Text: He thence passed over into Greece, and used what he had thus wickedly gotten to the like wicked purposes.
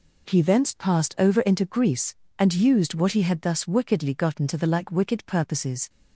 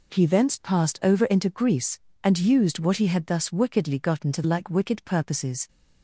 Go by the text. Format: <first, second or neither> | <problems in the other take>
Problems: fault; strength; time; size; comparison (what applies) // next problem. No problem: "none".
first | skips "the"; at 4.4 s